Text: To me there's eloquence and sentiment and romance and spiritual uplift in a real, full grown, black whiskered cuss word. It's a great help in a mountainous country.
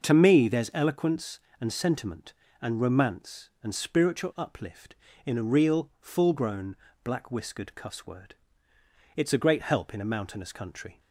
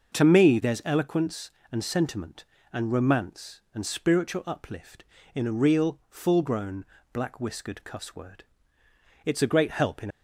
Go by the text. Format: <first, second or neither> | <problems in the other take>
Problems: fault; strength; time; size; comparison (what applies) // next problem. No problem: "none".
first | starts louder than the rest; until 1.2 s; 6.5 dB; also in the first // stops before "a mountainous country"; at 10.1 s